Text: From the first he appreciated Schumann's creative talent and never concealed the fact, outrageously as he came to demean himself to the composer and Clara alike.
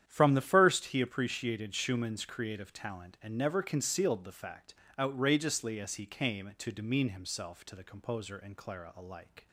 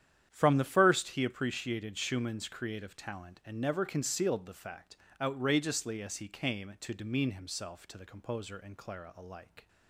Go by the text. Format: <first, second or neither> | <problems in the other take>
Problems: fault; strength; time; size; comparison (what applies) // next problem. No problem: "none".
neither | starts louder than the rest; strong; the same in both